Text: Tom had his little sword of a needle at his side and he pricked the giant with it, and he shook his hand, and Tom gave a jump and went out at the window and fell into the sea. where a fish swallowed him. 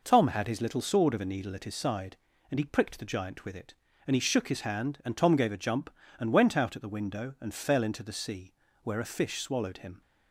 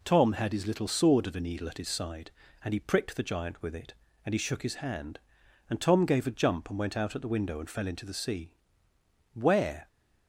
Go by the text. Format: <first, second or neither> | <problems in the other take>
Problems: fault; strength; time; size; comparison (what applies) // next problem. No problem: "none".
first | stops before "a fish swallowed him"; at 9.8 s